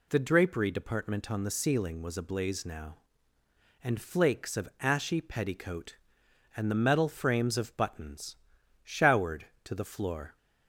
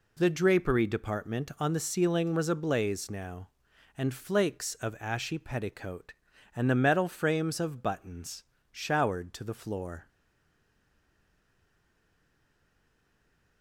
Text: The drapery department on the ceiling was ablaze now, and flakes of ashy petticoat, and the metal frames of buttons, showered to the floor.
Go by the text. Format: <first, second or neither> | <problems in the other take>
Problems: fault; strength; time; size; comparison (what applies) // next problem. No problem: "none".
first | stays silent after the last word; strong; from 10.0 s on; 3.6 s long